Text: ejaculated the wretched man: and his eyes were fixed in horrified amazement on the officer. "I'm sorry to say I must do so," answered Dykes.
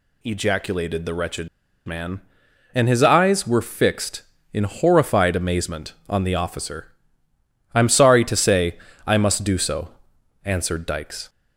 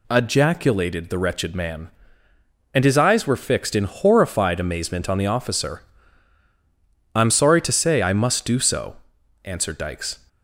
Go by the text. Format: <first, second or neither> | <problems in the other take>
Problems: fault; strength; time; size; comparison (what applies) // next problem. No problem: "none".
second | pauses between "wretched" and "man"; at 1.4 s; 0.38 s long // pauses between "say" and "I"; slight; at 8.7 s; 0.26 s long